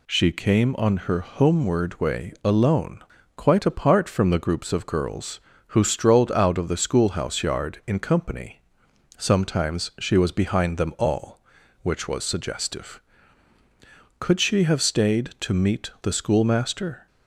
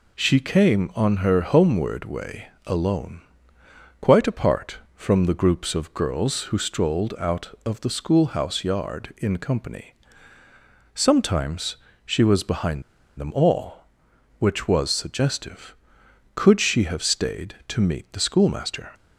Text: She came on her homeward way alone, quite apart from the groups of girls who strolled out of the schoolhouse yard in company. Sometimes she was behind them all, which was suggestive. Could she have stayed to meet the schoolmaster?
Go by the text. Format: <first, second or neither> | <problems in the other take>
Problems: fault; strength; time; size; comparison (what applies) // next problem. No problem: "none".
first | pauses between "way" and "alone"; slight; at 2.4 s; 0.18 s long // pauses between "Sometimes" and "she"; slight; at 11.7 s; 0.28 s long // pauses between "behind" and "them"; at 12.8 s; 0.37 s long